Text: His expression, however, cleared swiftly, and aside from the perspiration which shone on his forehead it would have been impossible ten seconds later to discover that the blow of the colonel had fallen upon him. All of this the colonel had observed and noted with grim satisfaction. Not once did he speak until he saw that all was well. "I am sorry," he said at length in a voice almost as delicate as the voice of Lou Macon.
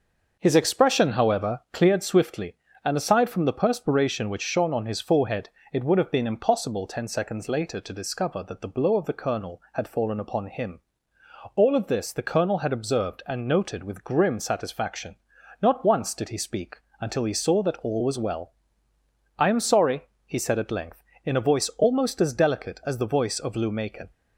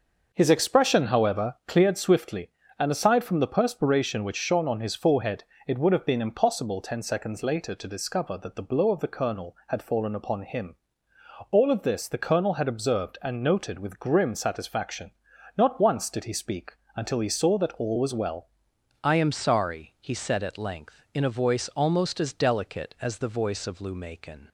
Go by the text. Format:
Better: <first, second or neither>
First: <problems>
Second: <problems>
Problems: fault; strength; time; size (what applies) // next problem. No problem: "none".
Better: first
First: starts louder than the rest; noticeable; until 1.4 s; 6 dB // pauses between "forehead" and "it"; slight; at 5.4 s; 0.24 s long // pauses between "speak" and "until"; slight; at 16.7 s; 0.24 s long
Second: starts louder than the rest; noticeable; until 1.3 s; 6 dB // pauses between "forehead" and "it"; slight; at 5.4 s; 0.24 s long // pauses between "speak" and "until"; slight; at 16.7 s; 0.24 s long // changes voice at "I"; from 19.0 s on; 5.4 s long